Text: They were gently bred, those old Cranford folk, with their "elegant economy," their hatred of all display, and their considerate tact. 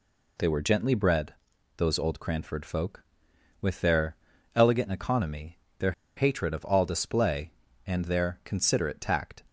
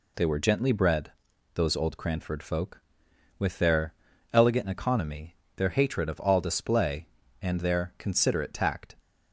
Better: second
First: pauses between "their" and "elegant"; at 4.1 s; 0.38 s long // pauses between "their" and "hatred"; slight; at 5.9 s; 0.24 s long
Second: pauses between "their" and "elegant"; at 3.9 s; 0.38 s long

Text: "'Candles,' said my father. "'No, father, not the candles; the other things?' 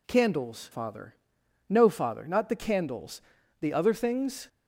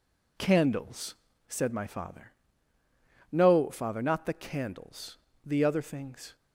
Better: second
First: skips "said my"; at 0.7 s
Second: none

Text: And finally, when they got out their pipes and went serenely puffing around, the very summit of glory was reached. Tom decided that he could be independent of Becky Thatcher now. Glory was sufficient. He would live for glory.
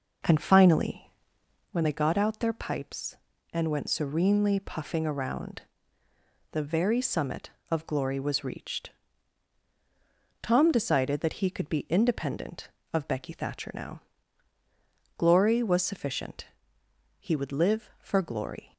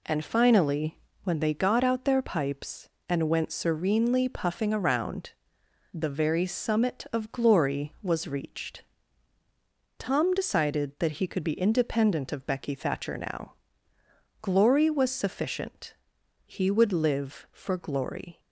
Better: second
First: starts louder than the rest; noticeable; until 1.8 s; 5 dB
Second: none

